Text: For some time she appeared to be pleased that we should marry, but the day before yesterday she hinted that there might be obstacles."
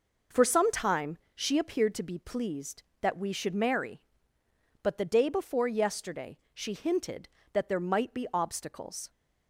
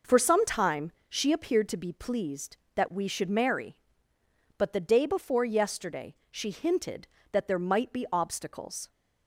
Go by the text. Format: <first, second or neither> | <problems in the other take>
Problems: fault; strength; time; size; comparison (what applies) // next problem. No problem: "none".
neither | pauses between "time" and "she"; slight; the same in both // pauses between "yesterday" and "she"; slight; the same in both